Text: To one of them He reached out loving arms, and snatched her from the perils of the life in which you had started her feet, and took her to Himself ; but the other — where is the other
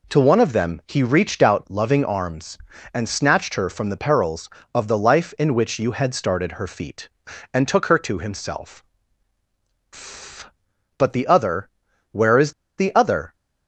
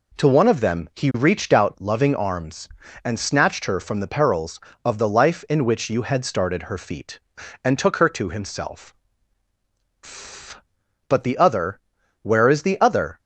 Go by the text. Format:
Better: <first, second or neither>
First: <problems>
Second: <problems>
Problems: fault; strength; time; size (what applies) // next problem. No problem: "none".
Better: second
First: pauses between "is" and "the"; slight; at 12.5 s; 0.27 s long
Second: none